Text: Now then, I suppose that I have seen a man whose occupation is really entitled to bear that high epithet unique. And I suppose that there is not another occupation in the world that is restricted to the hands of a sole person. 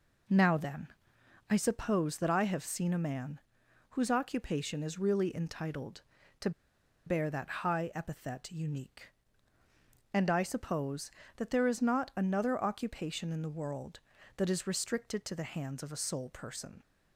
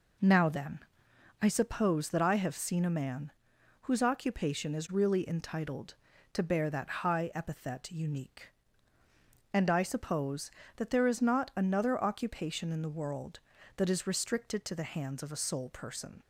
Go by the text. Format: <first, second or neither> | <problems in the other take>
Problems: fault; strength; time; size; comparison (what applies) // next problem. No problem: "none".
second | pauses between "man" and "whose"; noticeable; at 3.3 s; 0.52 s long; noticeable in the second // pauses between "to" and "bear"; noticeable; at 6.5 s; 0.56 s long